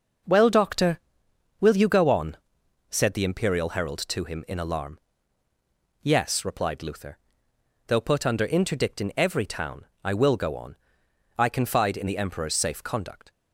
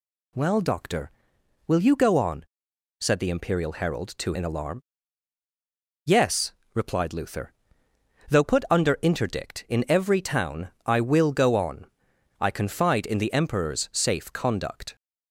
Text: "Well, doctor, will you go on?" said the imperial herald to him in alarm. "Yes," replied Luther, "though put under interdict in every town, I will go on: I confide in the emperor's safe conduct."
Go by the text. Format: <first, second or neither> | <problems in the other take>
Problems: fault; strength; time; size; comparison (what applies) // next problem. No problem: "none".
first | skips "him"; at 4.3 s